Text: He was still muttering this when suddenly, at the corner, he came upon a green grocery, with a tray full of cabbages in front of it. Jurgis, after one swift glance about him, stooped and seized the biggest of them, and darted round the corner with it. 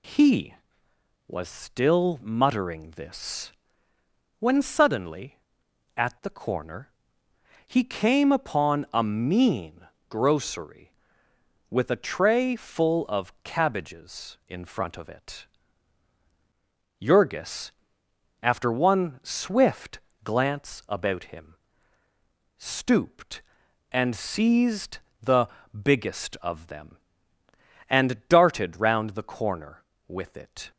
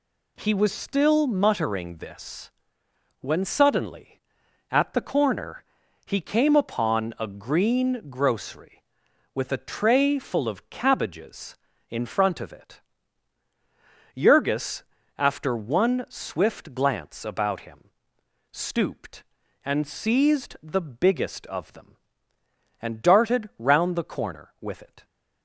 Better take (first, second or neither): second